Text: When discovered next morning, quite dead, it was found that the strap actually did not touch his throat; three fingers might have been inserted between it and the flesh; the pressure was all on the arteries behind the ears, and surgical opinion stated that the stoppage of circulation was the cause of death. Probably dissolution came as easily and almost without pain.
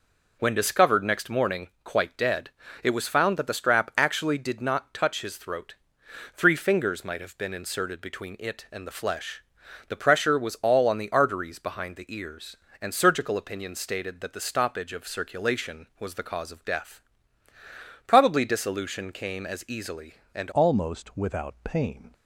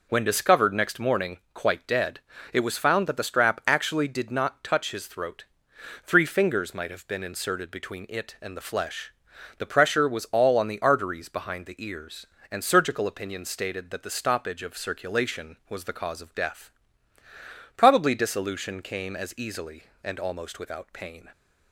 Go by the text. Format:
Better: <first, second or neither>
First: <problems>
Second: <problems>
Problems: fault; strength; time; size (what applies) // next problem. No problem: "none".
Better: second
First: changes voice at "almost"; from 20.5 s on; 1.6 s long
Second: none